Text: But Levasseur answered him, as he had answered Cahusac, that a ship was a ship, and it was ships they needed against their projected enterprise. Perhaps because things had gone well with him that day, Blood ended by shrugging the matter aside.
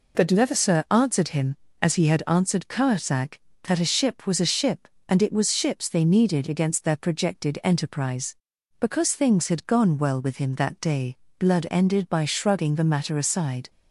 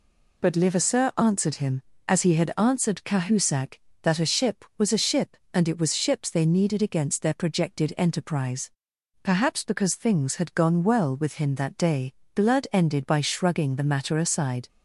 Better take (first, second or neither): second